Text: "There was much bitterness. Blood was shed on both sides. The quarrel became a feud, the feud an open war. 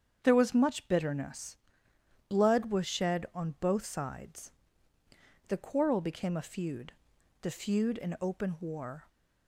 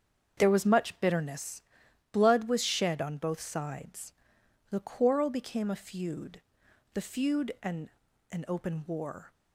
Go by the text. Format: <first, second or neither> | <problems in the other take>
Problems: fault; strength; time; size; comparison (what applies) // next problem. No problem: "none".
first | starts louder than the rest; strong; until 1.4 s; 7 dB; strong in the first // says "an" twice; at 8.3 s